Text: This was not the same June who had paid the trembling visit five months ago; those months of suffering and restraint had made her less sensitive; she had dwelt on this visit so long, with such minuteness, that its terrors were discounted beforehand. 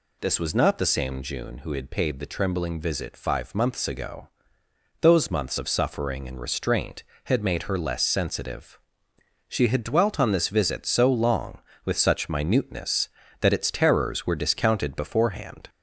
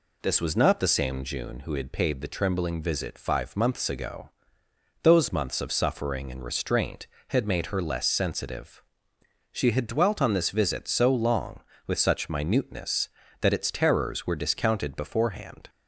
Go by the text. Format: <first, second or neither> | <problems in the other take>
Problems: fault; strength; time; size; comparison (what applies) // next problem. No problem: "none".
second | gets louder; slight; throughout; 2 dB